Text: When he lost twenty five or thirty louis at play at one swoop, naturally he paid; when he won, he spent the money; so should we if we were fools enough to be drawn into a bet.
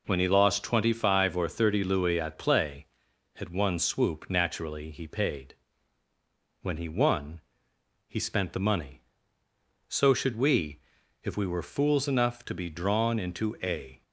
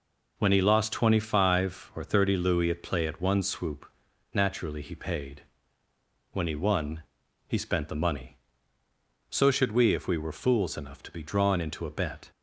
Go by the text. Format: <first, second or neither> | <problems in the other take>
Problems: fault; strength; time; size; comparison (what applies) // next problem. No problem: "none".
second | pauses between "we" and "if"; at 10.7 s; 0.44 s long // stops before "bet"; at 14.0 s